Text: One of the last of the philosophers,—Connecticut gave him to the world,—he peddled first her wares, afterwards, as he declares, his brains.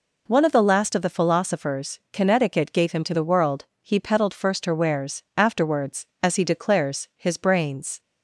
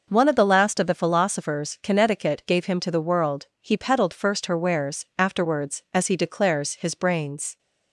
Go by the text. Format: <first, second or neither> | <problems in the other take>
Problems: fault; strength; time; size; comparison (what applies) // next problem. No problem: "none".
neither | none